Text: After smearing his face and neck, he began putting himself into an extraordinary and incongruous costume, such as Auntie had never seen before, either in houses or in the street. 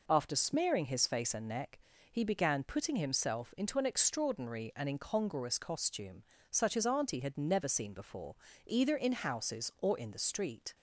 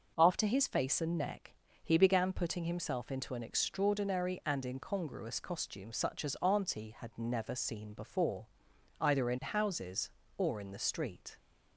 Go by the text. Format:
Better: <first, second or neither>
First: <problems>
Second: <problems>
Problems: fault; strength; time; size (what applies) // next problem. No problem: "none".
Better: first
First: none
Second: skips "smearing"; at 0.4 s